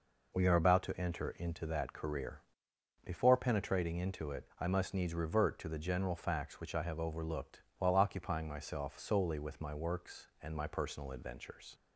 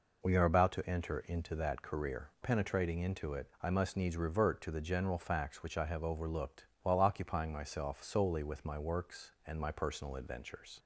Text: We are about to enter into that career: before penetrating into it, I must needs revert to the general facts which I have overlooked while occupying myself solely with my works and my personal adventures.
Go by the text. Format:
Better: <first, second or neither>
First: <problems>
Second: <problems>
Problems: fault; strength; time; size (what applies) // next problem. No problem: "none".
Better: first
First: pauses between "overlooked" and "while"; slight; at 7.6 s; 0.16 s long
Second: skips "before"; at 2.3 s // pauses between "overlooked" and "while"; slight; at 6.6 s; 0.16 s long